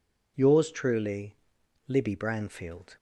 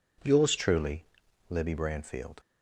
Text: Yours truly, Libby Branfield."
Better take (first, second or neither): first